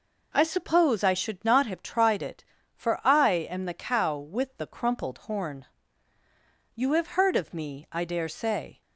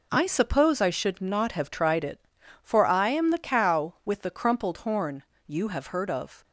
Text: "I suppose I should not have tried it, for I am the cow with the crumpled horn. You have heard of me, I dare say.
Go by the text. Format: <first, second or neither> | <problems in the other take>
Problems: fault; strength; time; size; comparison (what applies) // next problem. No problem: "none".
first | stops before "me I dare say"; at 6.4 s